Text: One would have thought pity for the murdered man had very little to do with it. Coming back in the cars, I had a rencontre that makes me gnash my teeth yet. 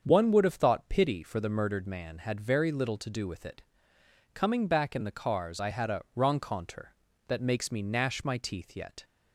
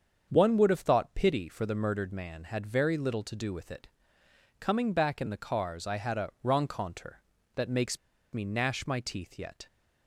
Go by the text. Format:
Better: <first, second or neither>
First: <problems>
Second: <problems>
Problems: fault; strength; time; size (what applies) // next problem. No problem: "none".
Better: first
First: starts louder than the rest; strong; until 1.0 s; 7 dB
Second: starts louder than the rest; strong; until 1.3 s; 7 dB // pauses between "makes" and "me"; slight; at 7.9 s; 0.35 s long